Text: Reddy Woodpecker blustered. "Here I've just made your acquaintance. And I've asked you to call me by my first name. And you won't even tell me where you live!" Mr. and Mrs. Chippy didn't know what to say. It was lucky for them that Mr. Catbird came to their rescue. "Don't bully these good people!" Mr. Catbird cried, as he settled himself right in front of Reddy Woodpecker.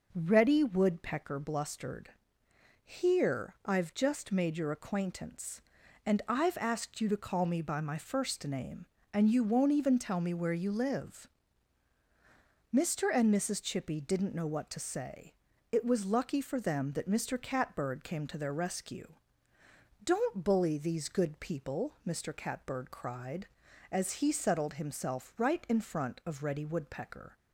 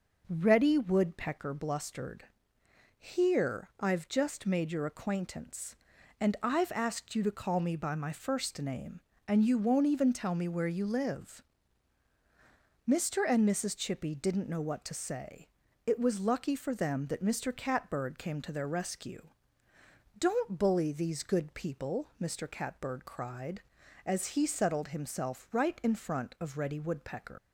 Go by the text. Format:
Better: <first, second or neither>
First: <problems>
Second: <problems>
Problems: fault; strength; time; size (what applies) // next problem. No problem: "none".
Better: first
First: none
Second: leaves "Woodpecker" unfinished; at 27.3 s; 135 ms